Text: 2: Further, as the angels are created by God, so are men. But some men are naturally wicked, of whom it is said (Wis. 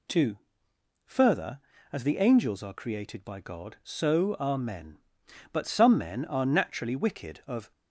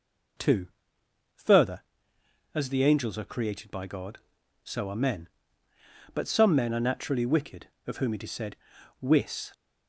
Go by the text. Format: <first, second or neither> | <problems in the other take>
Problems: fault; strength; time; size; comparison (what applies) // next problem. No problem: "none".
second | stops before "whom it is said Wis"; at 7.7 s